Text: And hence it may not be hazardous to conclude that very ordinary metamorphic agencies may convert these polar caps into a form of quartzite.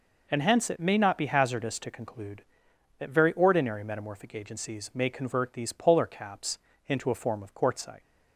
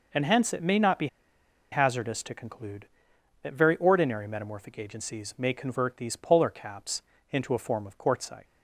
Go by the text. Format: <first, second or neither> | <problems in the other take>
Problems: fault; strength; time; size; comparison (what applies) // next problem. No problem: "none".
first | pauses between "be" and "hazardous"; noticeable; at 1.0 s; 0.65 s long // pauses between "caps" and "into"; slight; at 7.0 s; 0.30 s long; slight in the first